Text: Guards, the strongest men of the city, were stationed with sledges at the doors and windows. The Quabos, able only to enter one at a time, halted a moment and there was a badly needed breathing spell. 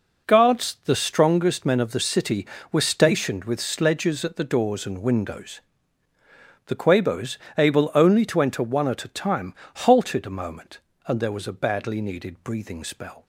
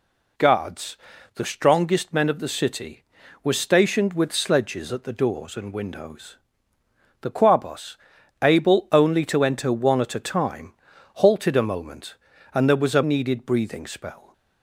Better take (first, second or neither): first